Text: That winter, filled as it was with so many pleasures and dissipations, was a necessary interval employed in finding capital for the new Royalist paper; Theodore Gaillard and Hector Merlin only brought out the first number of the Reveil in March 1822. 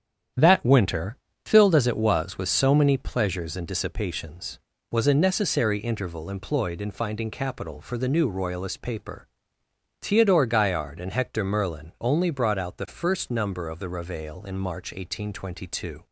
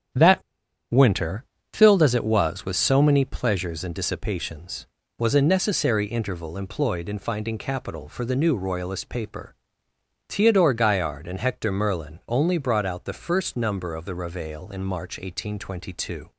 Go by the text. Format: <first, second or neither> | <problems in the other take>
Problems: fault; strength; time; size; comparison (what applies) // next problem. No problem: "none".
first | starts louder than the rest; strong; until 1.9 s; 9 dB; strong in the first // pauses between "That" and "winter"; noticeable; at 0.4 s; 0.49 s long